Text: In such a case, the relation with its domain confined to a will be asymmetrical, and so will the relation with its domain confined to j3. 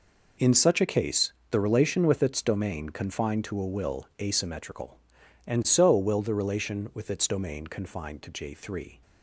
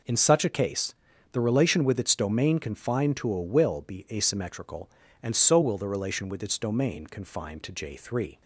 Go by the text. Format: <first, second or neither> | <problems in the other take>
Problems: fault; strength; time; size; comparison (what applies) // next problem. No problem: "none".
second | skips "be"; at 4.1 s